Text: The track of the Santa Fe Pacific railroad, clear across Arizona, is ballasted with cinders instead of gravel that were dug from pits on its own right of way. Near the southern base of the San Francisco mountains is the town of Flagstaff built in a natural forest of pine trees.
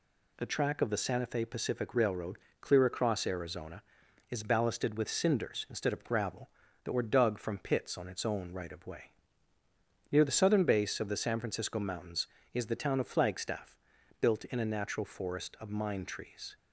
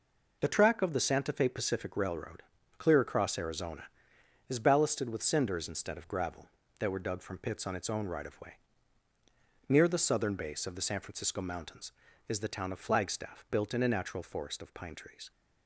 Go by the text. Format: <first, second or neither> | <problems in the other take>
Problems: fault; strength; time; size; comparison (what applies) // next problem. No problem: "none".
second | pauses between "Flagstaff" and "built"; at 13.7 s; 0.44 s long // says "mine" for "pine"; at 15.6 s